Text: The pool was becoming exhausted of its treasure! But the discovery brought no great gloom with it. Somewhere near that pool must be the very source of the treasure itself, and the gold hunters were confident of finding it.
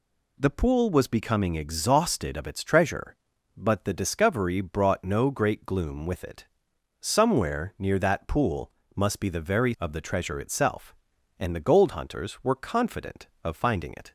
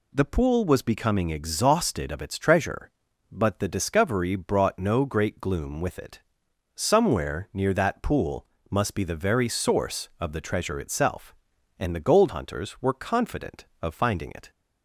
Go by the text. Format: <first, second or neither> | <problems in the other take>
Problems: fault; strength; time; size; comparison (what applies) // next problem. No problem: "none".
second | pauses between "pool" and "must"; slight; at 8.7 s; 0.24 s long; slight in the second // skips "source"; at 9.7 s